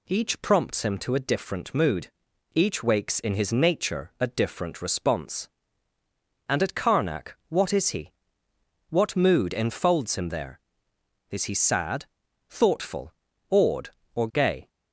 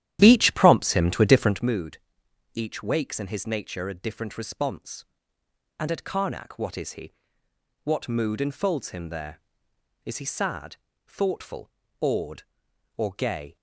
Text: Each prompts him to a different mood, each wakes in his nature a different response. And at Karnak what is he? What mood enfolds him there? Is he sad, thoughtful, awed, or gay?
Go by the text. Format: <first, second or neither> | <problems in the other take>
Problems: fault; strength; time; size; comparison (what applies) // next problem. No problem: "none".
first | starts louder than the rest; strong; until 1.7 s; 12 dB